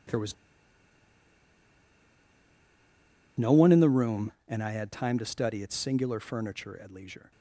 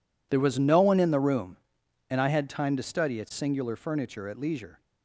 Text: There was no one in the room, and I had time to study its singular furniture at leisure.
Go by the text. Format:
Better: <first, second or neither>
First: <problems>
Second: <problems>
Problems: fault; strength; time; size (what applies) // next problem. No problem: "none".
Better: second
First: pauses between "was" and "no"; strong; at 0.3 s; 3.0 s long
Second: none